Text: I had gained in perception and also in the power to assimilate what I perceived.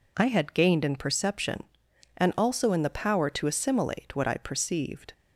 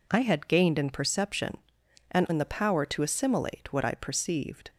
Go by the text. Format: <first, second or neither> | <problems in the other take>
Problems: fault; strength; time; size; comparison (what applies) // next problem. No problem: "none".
first | skips "also"; at 2.2 s